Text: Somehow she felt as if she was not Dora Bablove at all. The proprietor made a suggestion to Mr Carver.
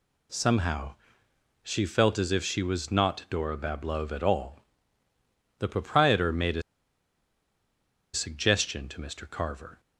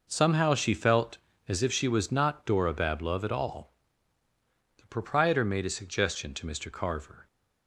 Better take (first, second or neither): second